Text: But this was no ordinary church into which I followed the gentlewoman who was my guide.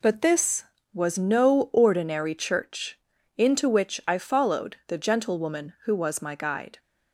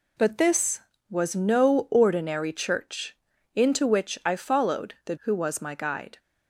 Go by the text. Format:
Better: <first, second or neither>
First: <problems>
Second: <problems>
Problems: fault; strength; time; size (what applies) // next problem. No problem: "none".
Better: first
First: pauses between "church" and "into"; at 2.9 s; 0.38 s long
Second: pauses between "church" and "into"; at 3.1 s; 0.38 s long // skips "gentlewoman"; at 5.1 s